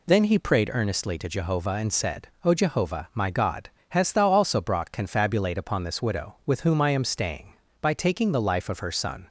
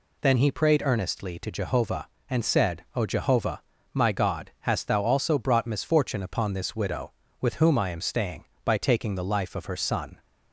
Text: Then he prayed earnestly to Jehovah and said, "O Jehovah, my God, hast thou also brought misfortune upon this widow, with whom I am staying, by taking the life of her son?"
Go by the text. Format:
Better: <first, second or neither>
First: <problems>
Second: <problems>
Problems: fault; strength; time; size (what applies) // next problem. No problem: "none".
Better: second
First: says "confabulate" for "misfortune"; at 4.9 s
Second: none